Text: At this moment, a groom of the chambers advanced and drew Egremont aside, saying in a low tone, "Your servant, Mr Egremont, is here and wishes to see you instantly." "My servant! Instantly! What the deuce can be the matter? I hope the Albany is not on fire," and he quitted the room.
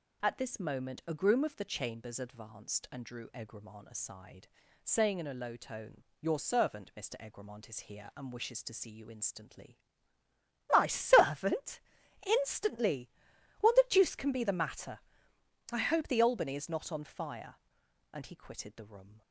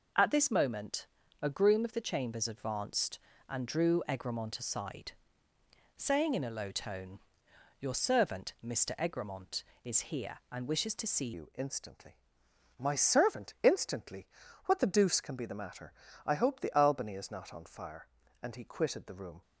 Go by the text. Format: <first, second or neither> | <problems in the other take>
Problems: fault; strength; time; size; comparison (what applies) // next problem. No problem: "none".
first | changes voice at "you"; from 11.3 s on; 8.1 s long